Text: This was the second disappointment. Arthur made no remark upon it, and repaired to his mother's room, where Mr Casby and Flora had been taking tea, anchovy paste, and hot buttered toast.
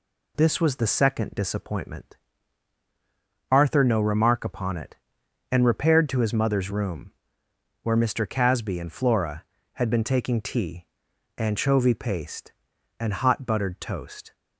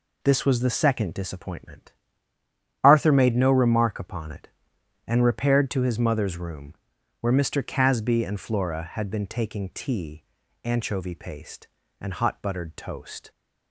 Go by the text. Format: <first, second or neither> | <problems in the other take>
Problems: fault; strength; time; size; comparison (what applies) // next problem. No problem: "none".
second | skips "made"; at 3.8 s